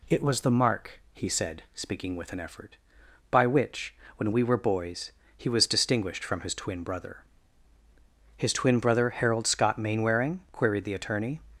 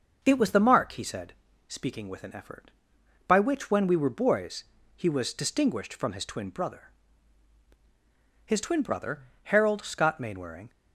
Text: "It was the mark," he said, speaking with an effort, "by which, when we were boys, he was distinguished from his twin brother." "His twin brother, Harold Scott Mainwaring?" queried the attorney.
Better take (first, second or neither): first